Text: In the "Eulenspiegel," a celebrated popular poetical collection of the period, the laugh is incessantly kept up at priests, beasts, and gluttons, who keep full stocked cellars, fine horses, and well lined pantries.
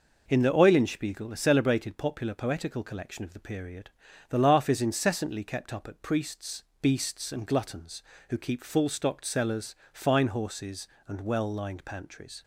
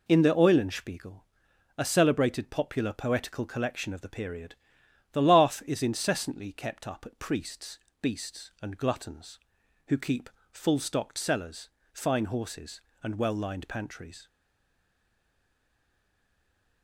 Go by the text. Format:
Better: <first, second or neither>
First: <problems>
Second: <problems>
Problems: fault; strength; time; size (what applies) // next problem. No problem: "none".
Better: first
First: none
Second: pauses between "keep" and "full"; slight; at 10.3 s; 0.22 s long // stays silent after the last word; strong; from 14.2 s on; 2.6 s long